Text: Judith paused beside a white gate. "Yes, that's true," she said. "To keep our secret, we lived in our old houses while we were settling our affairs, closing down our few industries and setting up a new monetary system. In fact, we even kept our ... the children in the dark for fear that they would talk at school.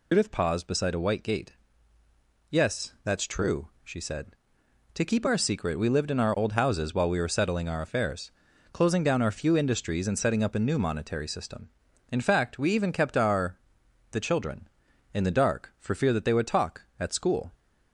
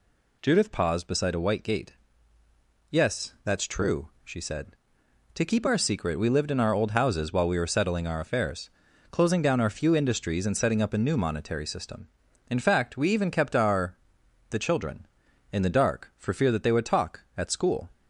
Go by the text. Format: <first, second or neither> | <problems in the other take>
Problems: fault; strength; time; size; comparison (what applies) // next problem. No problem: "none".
second | loses the start of "Judith"; at 0.1 s; 110 ms